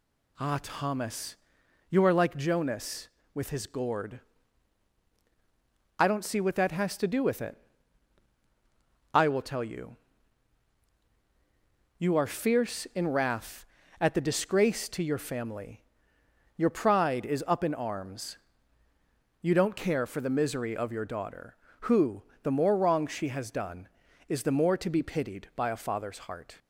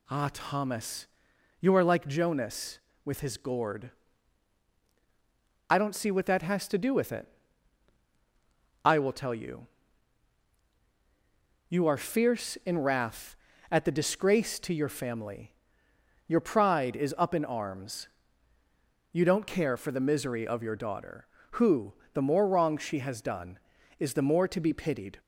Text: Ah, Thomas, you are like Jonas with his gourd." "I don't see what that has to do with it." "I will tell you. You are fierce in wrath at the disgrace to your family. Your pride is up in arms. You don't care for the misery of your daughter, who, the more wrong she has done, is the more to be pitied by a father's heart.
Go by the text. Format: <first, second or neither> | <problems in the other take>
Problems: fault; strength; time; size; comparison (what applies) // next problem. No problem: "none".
first | stops before "by a father's heart"; at 25.1 s